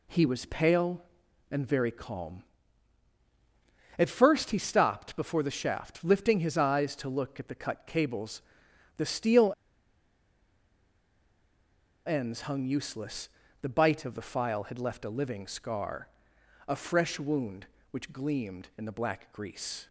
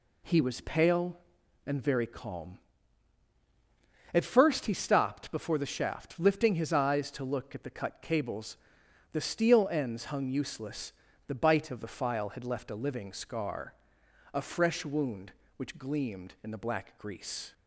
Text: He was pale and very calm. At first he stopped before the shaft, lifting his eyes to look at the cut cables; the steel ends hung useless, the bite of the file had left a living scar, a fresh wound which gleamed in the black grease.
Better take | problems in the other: second | pauses between "steel" and "ends"; strong; at 9.5 s; 2.5 s long

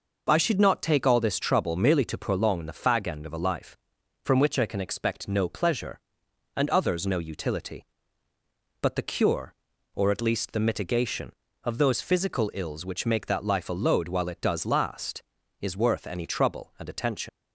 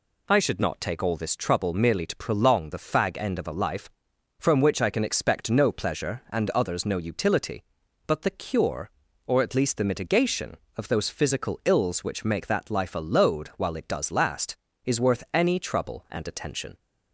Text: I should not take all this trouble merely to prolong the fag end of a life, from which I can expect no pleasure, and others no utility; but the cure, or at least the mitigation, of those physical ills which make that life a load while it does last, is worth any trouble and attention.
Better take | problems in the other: second | leaves "attention" unfinished; at 17.2 s; 90 ms

